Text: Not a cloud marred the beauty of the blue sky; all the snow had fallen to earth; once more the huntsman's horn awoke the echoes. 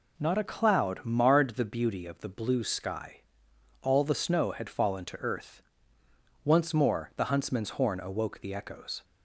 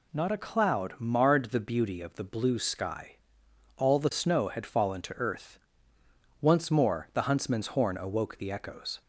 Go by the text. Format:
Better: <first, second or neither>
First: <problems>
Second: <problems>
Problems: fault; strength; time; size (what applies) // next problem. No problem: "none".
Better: second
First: starts louder than the rest; slight; until 1.5 s; 3 dB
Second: none